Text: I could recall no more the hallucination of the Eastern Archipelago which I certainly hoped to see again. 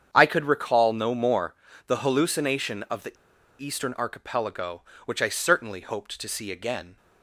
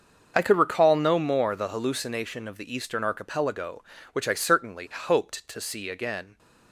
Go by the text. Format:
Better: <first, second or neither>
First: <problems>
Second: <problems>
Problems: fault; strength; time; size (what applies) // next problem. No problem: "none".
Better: second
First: starts louder than the rest; strong; until 1.1 s; 8 dB // pauses between "more" and "the"; slight; at 1.5 s; 0.32 s long // pauses between "the" and "Eastern"; at 3.1 s; 0.44 s long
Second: starts louder than the rest; until 1.3 s; 6.5 dB